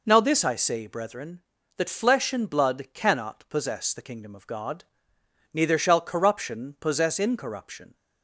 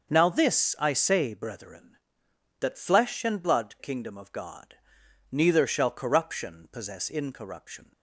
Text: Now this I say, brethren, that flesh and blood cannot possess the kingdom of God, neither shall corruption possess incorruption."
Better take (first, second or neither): first